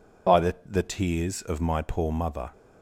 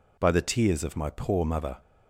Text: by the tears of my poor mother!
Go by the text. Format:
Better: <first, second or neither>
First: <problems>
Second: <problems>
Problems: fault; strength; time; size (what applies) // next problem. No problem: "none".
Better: second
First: says "the" twice; at 0.6 s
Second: none